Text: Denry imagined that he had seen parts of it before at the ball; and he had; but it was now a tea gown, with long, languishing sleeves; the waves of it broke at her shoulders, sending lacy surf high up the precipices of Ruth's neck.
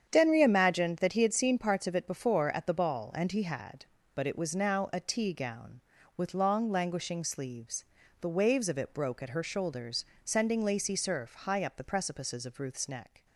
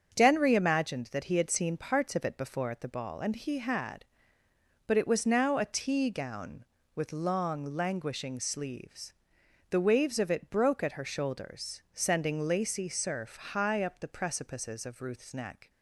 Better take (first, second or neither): neither